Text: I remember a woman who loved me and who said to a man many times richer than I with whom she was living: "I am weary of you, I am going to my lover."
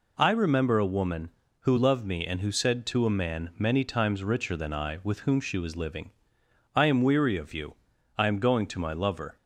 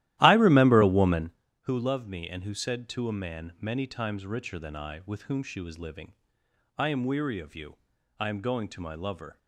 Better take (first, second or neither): first